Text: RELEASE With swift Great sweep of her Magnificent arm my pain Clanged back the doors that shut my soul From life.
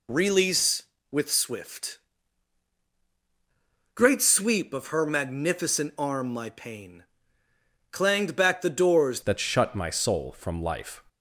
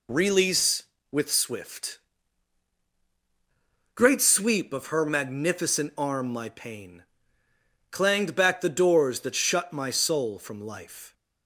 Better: second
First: pauses between "swift" and "Great"; strong; at 1.9 s; 1.9 s long // pauses between "pain" and "Clanged"; noticeable; at 7.0 s; 0.88 s long // changes voice at "that"; from 9.2 s on; 1.8 s long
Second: pauses between "swift" and "Great"; strong; at 1.9 s; 1.9 s long // pauses between "pain" and "Clanged"; noticeable; at 7.0 s; 0.88 s long

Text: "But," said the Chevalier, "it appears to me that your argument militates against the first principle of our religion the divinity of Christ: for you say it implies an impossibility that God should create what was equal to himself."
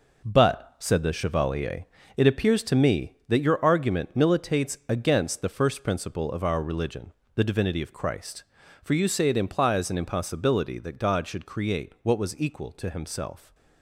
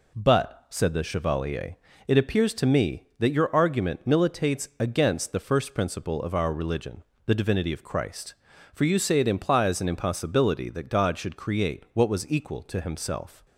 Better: second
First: gets quieter; throughout; 7 dB // pauses between "religion" and "the"; slight; at 7.1 s; 0.24 s long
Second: pauses between "religion" and "the"; slight; at 7.0 s; 0.24 s long

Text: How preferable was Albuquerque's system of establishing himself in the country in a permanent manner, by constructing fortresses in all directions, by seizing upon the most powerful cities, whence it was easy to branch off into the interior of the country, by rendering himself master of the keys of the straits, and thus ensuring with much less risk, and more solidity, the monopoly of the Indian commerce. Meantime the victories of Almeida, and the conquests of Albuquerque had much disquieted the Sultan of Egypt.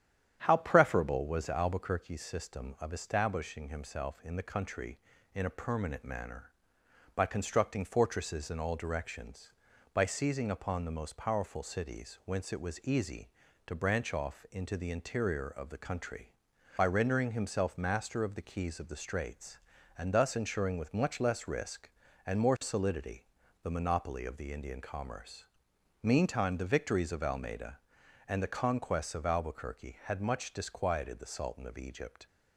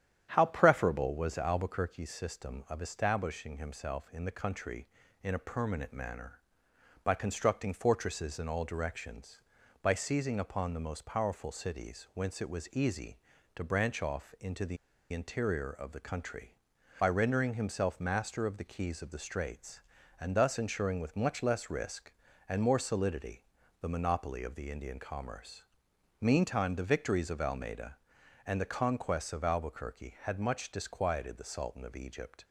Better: first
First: starts louder than the rest; strong; until 1.4 s; 9 dB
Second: starts louder than the rest; strong; until 1.3 s; 9 dB // pauses between "the" and "interior"; slight; at 14.7 s; 0.34 s long

